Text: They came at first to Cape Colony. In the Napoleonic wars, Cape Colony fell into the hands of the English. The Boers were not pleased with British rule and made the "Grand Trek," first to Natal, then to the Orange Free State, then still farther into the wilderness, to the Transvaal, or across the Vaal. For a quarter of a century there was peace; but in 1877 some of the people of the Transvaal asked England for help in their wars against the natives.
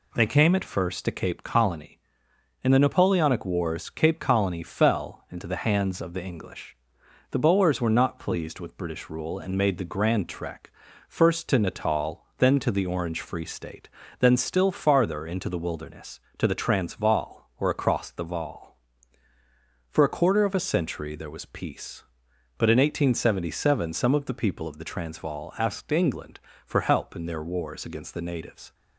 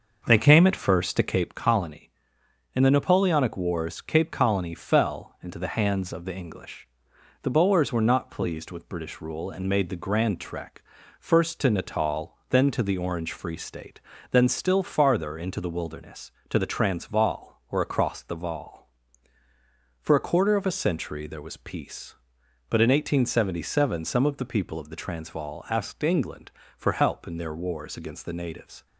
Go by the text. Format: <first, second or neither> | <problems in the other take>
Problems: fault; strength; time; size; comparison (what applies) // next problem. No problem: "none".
first | starts louder than the rest; noticeable; until 1.6 s; 6 dB